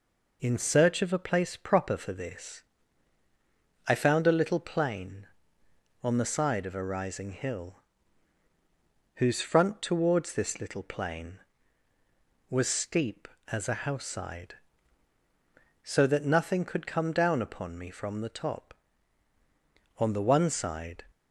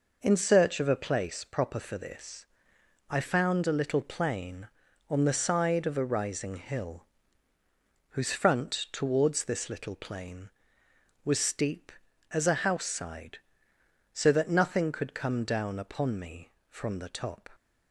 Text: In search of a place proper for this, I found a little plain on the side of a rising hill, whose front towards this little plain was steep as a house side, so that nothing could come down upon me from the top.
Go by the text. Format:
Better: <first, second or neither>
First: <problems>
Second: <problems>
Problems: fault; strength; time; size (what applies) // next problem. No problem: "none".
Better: second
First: goes on to say "On the one side"; noticeable; from 19.9 s on; 1.0 s long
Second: none